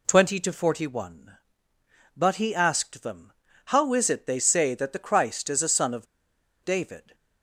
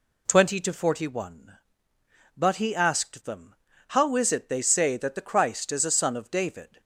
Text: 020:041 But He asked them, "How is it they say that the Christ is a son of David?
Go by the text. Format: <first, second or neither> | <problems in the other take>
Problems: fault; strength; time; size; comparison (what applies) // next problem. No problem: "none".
second | pauses between "of" and "David"; noticeable; at 6.0 s; 0.58 s long